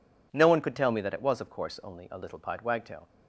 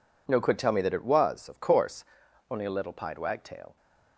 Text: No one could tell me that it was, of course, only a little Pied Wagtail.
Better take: first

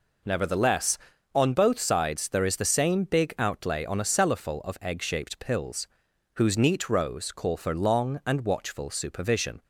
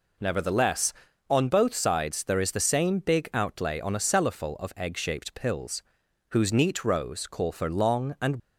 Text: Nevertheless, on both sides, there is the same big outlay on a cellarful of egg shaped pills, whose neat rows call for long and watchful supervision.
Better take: first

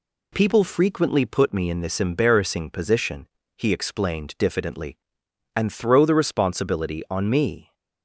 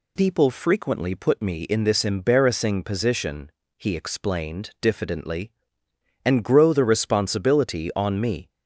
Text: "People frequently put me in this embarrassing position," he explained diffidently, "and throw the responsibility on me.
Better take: first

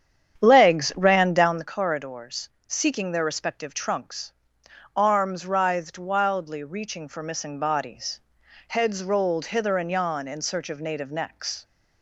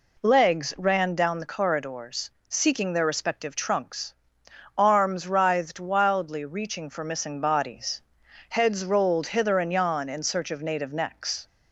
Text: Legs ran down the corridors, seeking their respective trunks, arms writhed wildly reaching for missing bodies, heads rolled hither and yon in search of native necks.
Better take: second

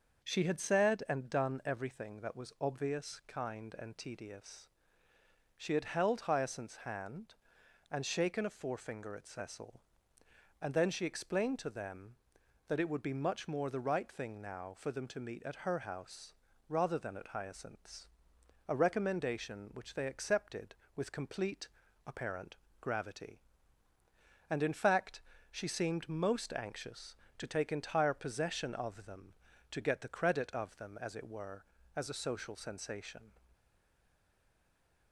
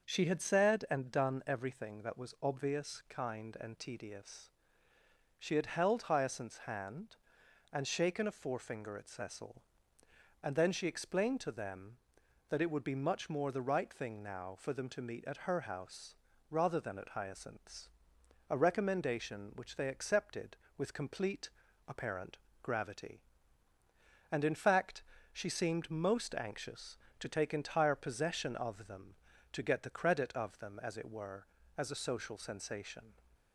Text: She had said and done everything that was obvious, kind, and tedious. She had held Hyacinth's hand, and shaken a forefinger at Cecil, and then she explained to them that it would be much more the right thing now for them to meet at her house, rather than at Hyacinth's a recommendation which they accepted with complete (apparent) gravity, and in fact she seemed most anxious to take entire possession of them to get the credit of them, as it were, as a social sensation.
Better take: second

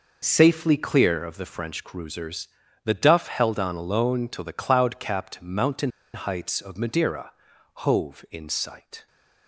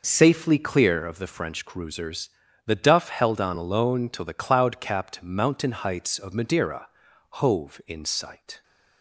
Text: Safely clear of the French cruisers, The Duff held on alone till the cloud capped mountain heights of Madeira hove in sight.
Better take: second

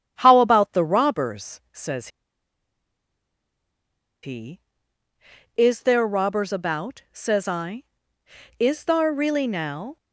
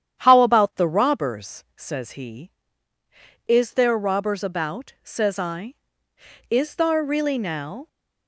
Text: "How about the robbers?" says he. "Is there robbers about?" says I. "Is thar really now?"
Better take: second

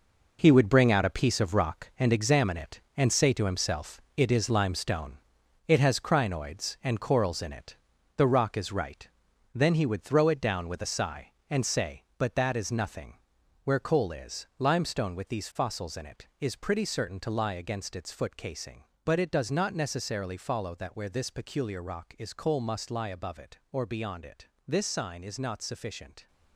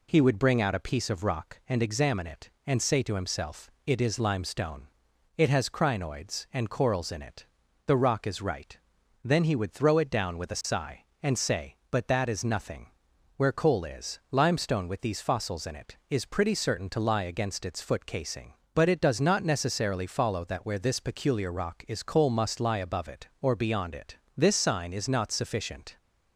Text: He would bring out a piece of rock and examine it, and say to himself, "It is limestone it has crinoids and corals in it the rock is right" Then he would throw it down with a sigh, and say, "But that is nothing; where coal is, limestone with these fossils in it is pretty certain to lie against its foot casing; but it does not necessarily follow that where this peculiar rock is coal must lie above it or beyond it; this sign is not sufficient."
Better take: second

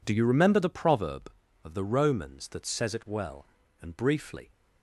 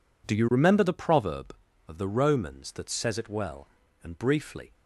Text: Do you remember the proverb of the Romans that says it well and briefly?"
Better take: neither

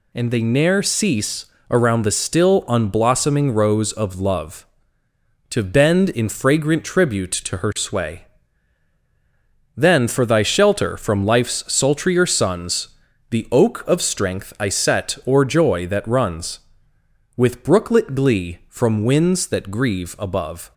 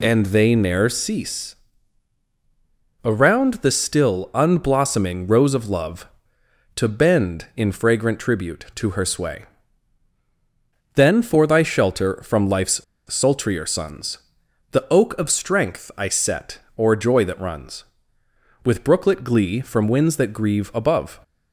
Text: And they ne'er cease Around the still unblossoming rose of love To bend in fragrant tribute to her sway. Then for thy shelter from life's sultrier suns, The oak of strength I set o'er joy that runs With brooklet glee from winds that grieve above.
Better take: first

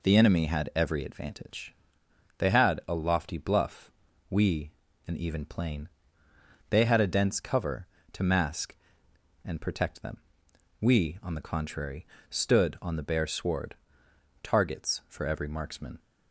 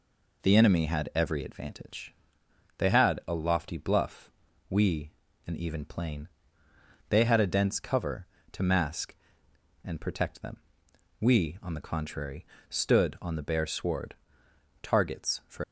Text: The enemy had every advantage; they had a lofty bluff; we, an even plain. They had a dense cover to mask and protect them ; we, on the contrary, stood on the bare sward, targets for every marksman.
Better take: first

